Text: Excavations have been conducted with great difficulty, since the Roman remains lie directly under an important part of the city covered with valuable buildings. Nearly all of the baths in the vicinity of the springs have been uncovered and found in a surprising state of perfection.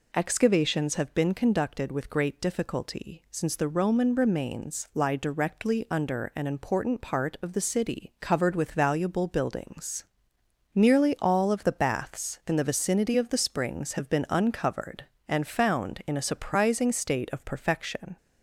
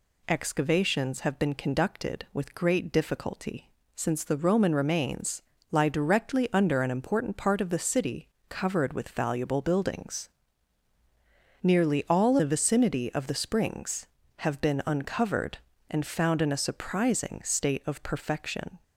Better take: first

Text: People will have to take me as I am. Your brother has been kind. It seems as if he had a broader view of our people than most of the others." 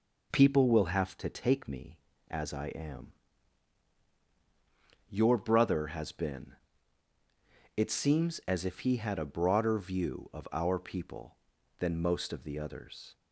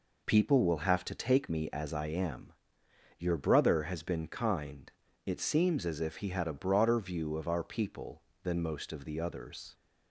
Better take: second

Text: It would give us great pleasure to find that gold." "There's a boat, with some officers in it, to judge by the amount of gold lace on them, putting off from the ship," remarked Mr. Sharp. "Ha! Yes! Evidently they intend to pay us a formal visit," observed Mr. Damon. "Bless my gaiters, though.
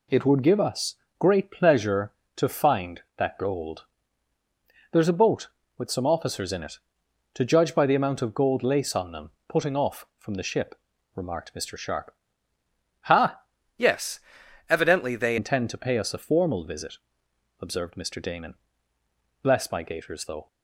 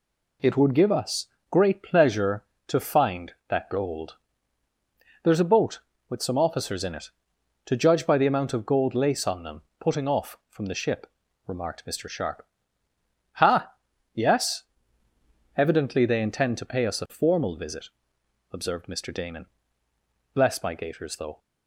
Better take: second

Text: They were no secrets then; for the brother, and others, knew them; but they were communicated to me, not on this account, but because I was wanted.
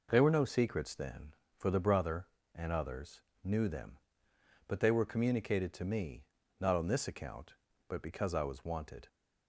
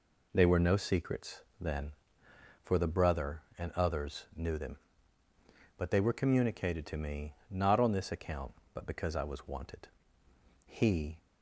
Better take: first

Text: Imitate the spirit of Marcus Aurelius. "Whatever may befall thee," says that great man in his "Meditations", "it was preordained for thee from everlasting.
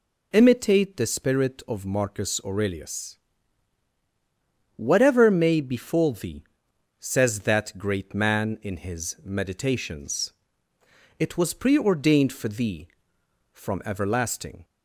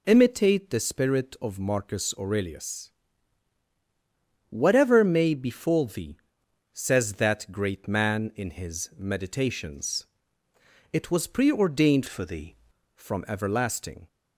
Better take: first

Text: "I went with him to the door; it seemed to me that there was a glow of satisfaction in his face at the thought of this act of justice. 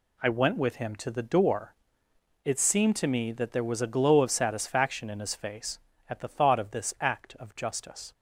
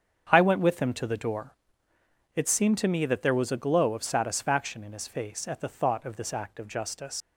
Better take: first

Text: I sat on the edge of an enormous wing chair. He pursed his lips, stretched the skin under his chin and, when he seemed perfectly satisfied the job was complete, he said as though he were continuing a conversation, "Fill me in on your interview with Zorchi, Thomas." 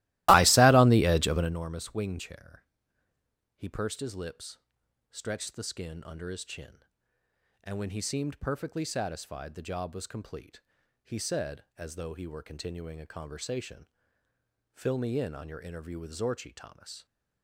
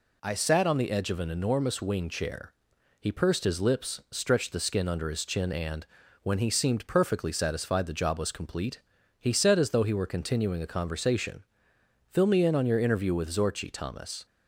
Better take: second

